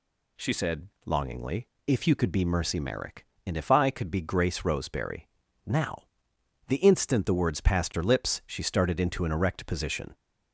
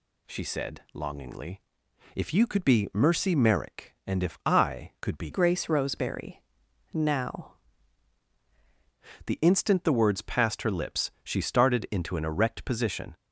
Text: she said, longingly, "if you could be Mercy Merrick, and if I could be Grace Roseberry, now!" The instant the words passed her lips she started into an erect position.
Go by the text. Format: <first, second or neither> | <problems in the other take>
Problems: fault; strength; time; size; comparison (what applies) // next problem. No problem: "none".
first | changes voice from "Grace" to "now"; from 5.3 to 7.5 s; 2.2 s long